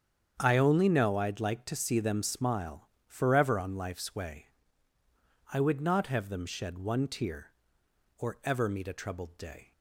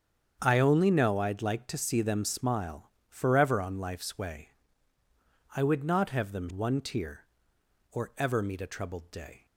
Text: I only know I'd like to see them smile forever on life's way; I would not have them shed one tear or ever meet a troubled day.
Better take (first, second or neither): first